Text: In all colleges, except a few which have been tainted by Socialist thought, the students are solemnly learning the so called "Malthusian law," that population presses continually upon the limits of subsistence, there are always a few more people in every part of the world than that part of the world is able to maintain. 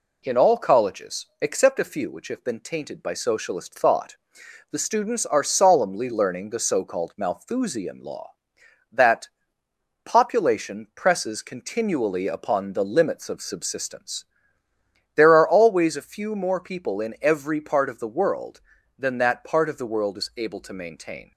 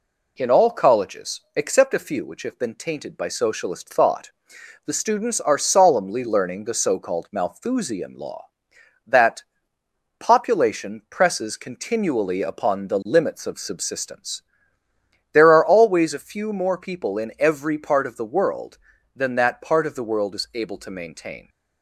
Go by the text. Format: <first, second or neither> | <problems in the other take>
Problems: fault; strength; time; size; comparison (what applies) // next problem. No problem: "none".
neither | pauses between "that" and "population"; noticeable; the same in both